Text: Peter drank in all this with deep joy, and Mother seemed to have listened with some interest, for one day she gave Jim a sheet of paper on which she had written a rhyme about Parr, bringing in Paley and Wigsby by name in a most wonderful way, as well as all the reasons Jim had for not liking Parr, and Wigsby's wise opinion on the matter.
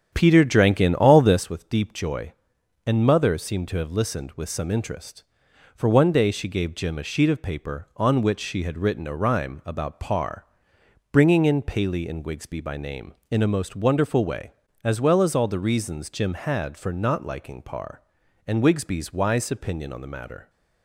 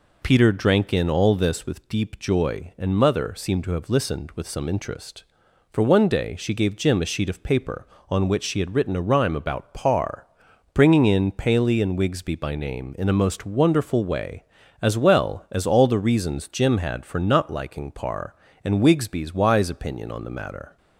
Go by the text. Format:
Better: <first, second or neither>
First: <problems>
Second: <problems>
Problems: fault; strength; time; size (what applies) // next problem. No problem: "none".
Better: second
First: starts louder than the rest; strong; until 1.4 s; 8.5 dB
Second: none